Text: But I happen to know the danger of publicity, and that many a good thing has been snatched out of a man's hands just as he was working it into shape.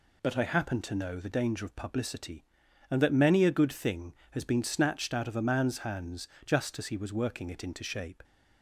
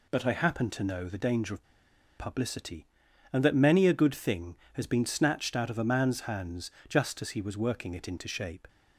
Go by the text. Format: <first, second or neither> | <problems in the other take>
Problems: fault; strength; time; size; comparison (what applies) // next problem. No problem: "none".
first | pauses between "of" and "publicity"; noticeable; at 1.6 s; 0.54 s long // pauses between "hands" and "just"; slight; at 6.6 s; 0.18 s long; slight in the first